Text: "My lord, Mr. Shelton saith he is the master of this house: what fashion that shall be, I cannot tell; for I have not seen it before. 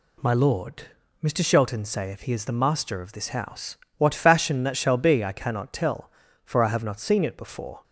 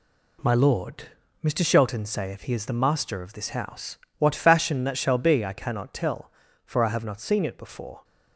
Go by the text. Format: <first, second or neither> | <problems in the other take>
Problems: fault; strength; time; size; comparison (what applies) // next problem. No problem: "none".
first | gets quieter; throughout; 6.5 dB